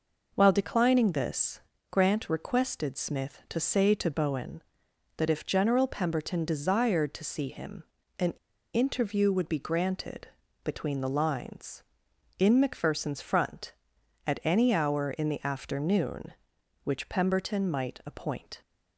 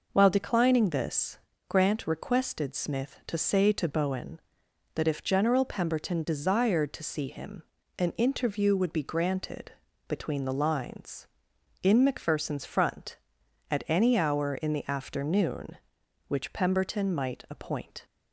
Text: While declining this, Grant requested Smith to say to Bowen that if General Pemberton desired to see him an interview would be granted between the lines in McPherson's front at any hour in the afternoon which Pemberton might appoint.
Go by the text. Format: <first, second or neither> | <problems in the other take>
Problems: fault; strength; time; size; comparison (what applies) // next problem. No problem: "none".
second | pauses between "him" and "an"; slight; at 7.8 s; 0.34 s long; slight in the second // pauses between "an" and "interview"; at 8.3 s; 0.40 s long // pauses between "granted" and "between"; slight; at 10.2 s; 0.34 s long; slight in the second